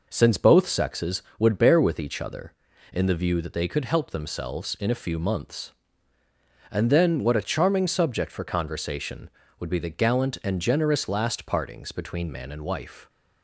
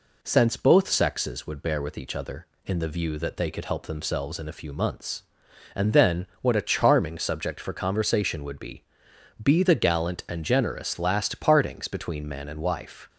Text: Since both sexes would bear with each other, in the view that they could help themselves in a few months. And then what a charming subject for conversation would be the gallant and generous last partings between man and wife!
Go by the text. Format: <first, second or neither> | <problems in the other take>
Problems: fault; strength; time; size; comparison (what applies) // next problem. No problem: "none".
first | says "be" twice; at 9.4 s